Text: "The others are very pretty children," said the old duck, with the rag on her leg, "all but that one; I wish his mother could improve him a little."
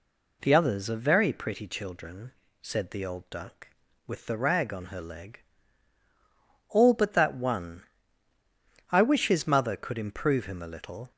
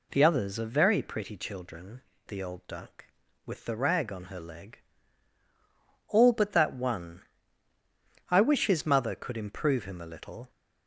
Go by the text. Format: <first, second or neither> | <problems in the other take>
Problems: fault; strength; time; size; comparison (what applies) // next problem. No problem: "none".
first | skips "said"; at 2.1 s